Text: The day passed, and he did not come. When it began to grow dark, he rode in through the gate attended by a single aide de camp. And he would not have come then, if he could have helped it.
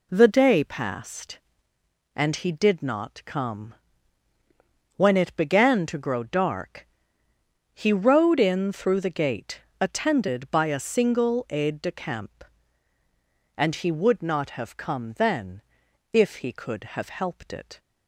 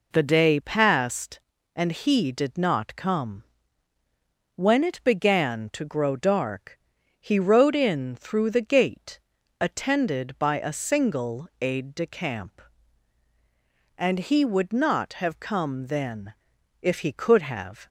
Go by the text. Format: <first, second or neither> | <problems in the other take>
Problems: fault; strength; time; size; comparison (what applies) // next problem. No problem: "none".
first | pauses between "gate" and "attended"; at 9.1 s; 0.40 s long; slight in the first // stops before "helped it"; at 17.8 s